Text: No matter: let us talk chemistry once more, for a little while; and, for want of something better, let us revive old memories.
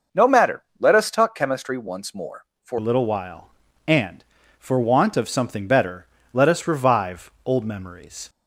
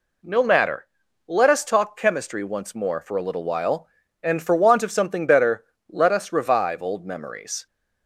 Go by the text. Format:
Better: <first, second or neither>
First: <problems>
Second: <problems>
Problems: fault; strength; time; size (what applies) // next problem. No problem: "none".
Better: second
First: changes voice at "a"; from 2.7 s on; 5.5 s long // pauses between "revive" and "old"; slight; at 7.2 s; 0.16 s long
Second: none